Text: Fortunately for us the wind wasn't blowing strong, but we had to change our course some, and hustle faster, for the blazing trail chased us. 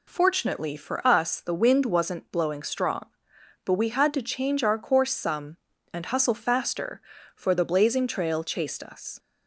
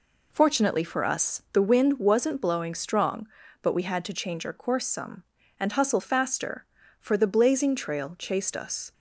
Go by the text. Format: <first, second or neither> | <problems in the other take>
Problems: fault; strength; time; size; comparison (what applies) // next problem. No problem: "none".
neither | none